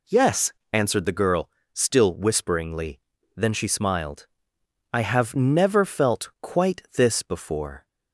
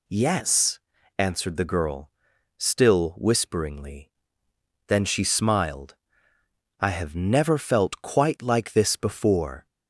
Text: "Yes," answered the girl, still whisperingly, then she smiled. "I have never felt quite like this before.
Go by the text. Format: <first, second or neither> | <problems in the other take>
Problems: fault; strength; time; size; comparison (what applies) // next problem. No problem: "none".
second | skips "like"; at 6.8 s